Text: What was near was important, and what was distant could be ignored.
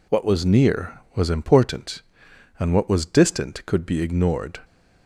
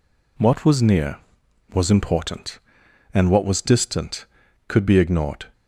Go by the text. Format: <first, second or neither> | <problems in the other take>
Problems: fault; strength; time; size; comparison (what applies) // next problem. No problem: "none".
neither | none